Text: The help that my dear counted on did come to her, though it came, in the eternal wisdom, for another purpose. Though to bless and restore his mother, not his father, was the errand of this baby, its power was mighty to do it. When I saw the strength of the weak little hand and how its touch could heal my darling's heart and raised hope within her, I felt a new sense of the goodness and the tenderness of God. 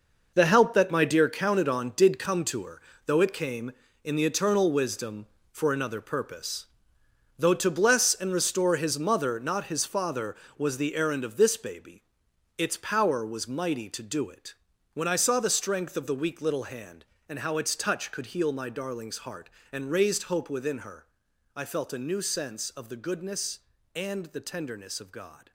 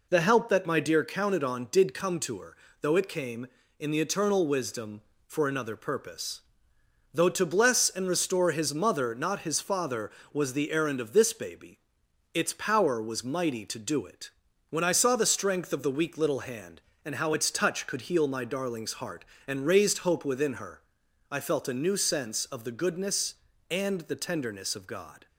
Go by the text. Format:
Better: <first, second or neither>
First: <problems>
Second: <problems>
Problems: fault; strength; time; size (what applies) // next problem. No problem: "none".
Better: second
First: gets quieter; strong; throughout; 10.5 dB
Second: none